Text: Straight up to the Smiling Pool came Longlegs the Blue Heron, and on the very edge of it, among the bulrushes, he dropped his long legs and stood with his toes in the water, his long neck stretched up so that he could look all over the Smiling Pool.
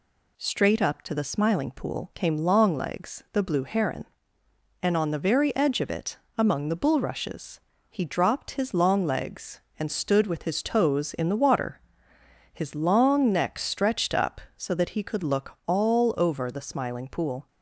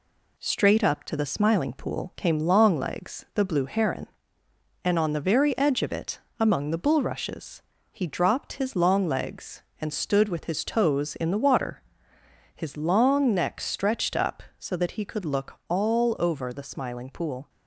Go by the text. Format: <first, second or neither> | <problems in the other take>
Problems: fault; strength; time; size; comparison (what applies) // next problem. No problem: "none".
first | gets quieter; slight; throughout; 2.5 dB